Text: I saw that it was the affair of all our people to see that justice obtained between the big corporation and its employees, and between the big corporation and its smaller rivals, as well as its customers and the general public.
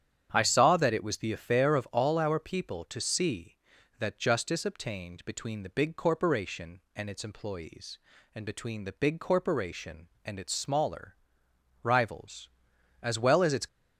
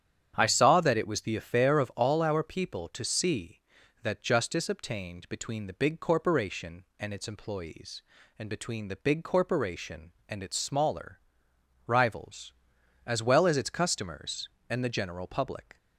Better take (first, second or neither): second